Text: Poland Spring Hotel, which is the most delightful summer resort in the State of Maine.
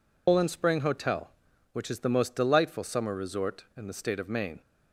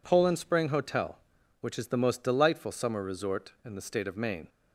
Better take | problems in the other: second | loses the start of "Poland"; at 0.2 s; 120 ms

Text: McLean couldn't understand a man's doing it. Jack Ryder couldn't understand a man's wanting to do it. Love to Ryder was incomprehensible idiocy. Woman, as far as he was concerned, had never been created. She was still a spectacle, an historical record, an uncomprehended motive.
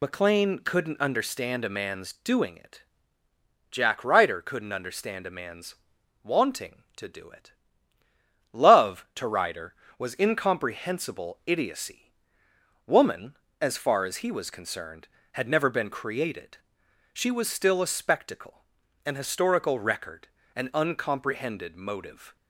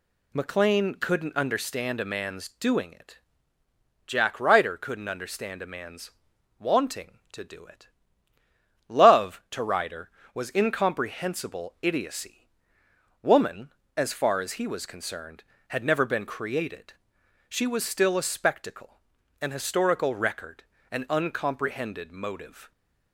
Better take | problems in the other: second | loses the start of "McLean"; at 0.0 s; 40 ms // pauses between "man's" and "wanting"; noticeable; at 5.7 s; 0.48 s long; noticeable in the second

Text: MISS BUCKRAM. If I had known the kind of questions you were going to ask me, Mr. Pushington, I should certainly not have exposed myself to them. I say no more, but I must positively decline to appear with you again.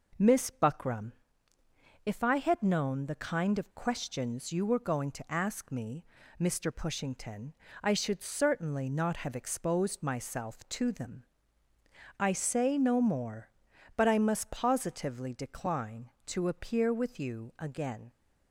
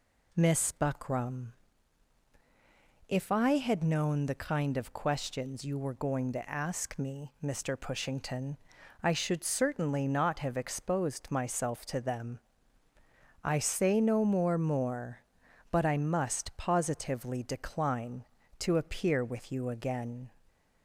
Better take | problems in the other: first | says "more" twice; at 14.5 s

